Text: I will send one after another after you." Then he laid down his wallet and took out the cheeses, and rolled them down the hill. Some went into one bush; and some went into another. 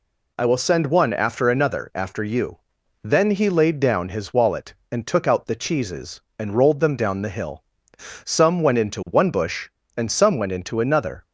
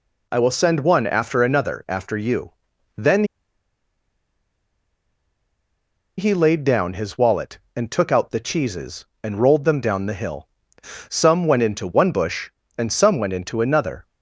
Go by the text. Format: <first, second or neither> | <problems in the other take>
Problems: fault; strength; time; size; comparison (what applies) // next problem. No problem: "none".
first | pauses between "Then" and "he"; strong; at 3.2 s; 2.9 s long